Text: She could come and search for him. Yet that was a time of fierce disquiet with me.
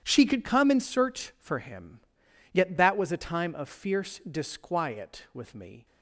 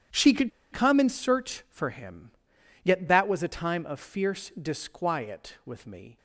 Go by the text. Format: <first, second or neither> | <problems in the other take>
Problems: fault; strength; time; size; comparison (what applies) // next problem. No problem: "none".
first | starts louder than the rest; strong; until 1.3 s; 9.5 dB; strong in the first // pauses between "could" and "come"; slight; at 0.5 s; 0.22 s long